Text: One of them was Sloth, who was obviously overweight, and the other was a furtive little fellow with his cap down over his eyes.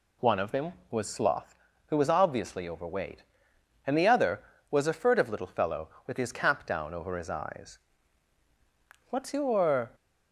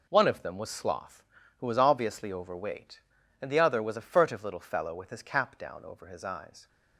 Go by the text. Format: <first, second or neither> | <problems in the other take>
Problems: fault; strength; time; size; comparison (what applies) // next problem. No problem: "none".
second | goes on to say "What's your"; noticeable; from 9.0 s on; 0.82 s long